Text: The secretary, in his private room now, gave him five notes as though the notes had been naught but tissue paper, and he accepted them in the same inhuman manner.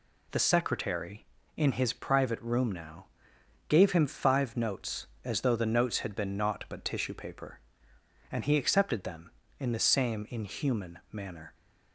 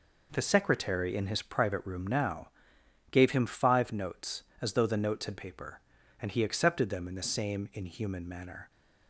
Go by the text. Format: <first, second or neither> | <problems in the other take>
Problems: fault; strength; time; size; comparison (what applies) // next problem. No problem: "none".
first | skips "been naught but tissue"; at 5.3 s